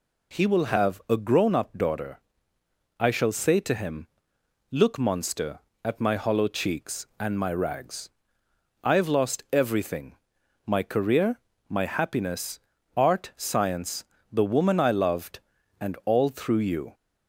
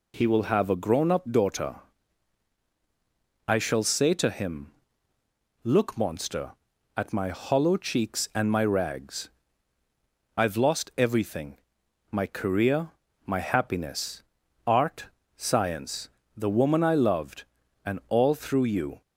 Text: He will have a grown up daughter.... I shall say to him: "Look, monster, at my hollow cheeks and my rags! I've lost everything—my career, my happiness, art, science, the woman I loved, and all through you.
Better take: neither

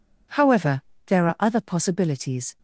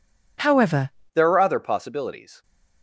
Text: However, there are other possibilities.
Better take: first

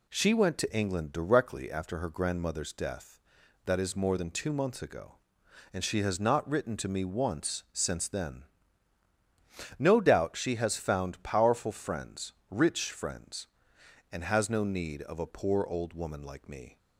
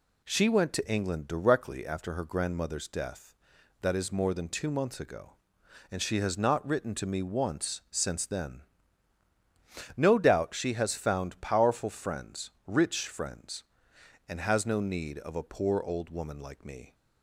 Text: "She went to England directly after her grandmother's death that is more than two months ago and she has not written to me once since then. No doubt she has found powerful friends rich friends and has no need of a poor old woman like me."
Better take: neither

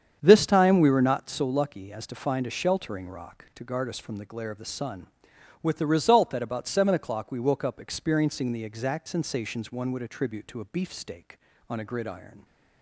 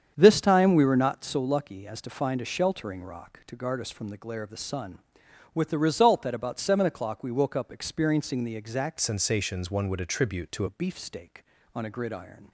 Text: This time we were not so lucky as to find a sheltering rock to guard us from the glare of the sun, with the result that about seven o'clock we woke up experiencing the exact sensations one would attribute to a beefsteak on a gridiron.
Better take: first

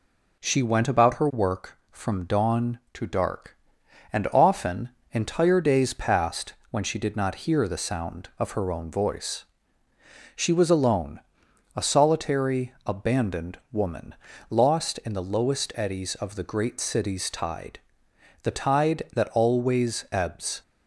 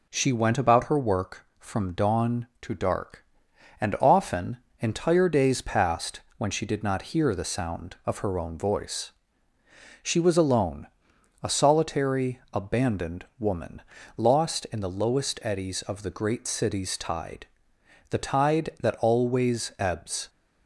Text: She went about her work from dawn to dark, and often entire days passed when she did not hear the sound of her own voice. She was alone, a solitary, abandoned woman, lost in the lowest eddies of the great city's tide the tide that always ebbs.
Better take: neither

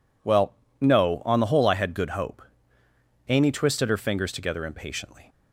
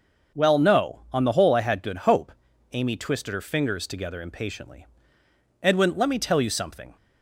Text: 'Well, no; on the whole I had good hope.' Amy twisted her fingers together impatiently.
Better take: first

